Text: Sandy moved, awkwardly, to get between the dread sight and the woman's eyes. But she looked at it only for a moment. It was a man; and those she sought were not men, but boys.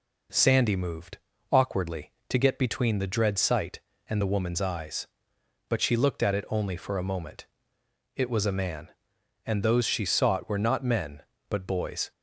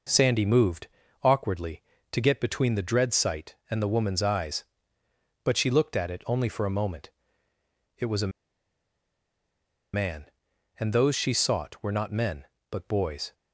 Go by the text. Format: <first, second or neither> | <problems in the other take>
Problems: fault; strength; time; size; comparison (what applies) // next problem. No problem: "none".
first | pauses between "a" and "man"; strong; at 8.3 s; 1.6 s long